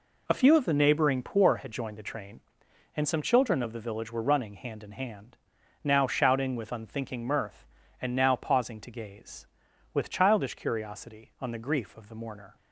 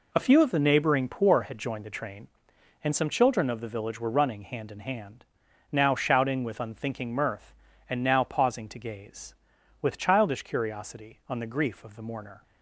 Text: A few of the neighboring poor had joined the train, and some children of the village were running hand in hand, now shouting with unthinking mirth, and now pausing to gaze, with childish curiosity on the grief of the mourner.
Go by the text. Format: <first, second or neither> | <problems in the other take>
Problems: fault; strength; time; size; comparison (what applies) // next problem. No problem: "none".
neither | none